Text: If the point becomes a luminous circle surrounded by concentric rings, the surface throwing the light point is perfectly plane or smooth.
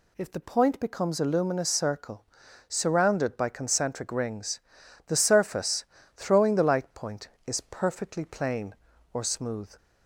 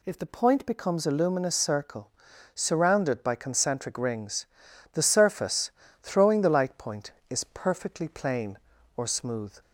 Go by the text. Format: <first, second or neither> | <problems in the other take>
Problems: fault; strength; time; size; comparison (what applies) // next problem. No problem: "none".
neither | pauses between "circle" and "surrounded"; the same in both // pauses between "surface" and "throwing"; slight; the same in both